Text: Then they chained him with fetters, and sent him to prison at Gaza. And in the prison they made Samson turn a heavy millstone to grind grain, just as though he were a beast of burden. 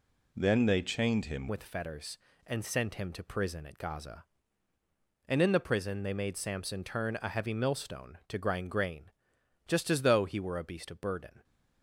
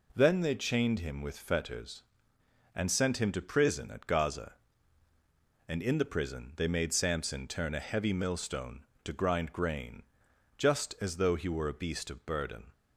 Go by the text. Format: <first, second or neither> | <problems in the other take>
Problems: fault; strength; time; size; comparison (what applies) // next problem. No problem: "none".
second | changes voice at "with"; from 1.4 s on; 10.0 s long